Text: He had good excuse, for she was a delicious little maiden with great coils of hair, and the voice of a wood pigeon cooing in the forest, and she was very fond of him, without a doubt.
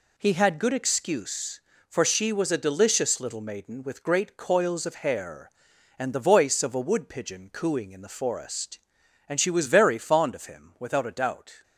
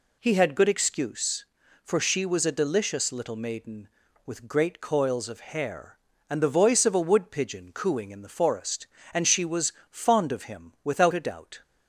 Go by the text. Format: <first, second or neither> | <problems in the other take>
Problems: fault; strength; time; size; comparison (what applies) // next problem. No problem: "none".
first | skips "very"; at 9.8 s